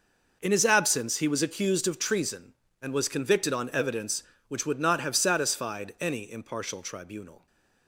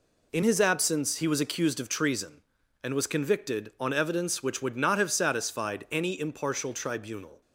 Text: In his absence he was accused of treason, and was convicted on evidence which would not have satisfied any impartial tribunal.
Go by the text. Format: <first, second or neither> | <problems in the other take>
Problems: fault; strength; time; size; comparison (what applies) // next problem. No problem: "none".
neither | none